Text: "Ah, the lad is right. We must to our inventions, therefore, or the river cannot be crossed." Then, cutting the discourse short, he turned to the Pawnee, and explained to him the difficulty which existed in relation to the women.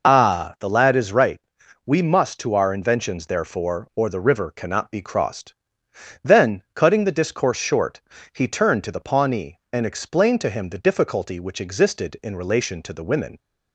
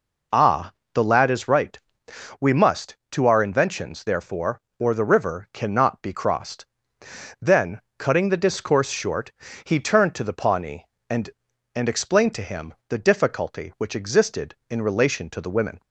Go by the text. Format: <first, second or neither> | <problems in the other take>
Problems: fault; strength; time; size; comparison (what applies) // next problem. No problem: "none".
first | says "and" twice; at 11.7 s // pauses between "him" and "the"; slight; at 12.7 s; 0.16 s long